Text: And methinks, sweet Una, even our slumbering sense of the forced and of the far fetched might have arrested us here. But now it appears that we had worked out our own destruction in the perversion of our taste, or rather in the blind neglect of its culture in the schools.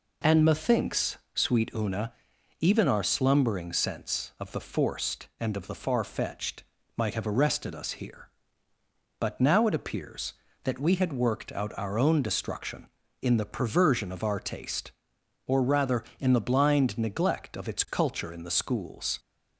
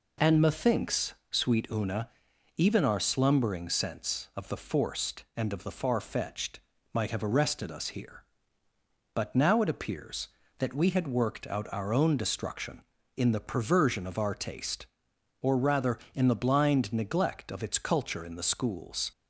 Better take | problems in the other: neither | pauses between "fetched" and "might"; slight; the same in both

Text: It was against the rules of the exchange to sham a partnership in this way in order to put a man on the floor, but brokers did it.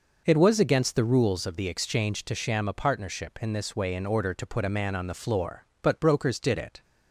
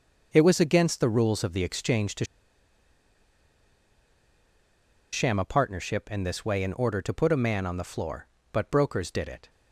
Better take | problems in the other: first | pauses between "to" and "sham"; strong; at 2.2 s; 2.8 s long

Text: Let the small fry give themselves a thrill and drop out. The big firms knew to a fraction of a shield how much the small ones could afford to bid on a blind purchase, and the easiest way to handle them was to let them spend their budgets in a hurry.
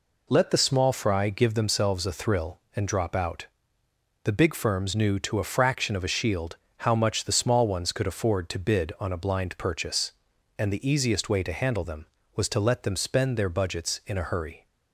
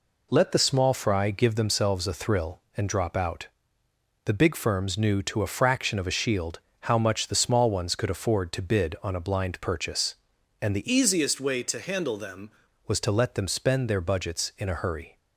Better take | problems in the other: first | pauses between "shield" and "how"; slight; at 6.5 s; 0.20 s long; slight in the first // changes voice from "easiest" to "them"; from 10.9 to 12.5 s; 1.6 s long

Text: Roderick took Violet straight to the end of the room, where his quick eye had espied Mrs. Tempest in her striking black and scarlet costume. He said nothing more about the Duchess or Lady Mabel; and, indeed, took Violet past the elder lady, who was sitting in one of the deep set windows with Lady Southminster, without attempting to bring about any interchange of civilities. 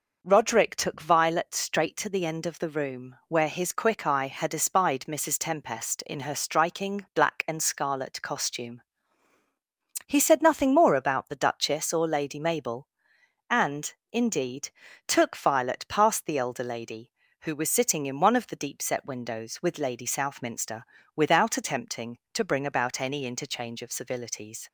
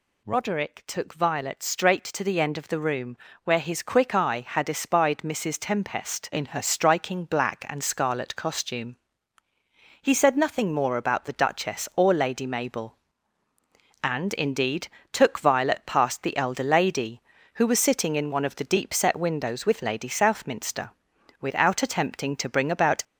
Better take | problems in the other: first | stops before "any interchange of civilities"; at 23.0 s

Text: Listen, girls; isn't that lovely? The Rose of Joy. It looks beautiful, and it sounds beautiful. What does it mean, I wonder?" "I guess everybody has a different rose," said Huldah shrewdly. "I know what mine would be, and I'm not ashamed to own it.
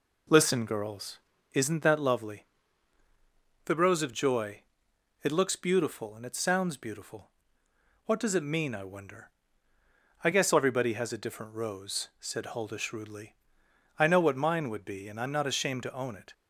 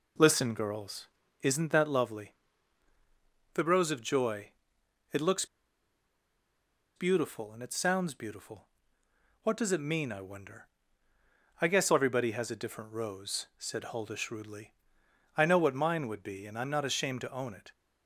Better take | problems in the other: first | pauses between "looks" and "beautiful"; strong; at 5.4 s; 1.5 s long

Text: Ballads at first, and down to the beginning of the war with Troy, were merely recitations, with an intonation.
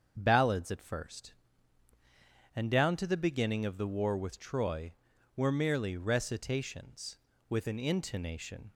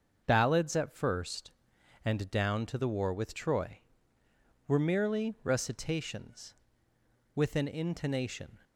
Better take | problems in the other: first | starts louder than the rest; until 1.2 s; 6.5 dB; also in the first // skips "beginning of the"; at 2.8 s

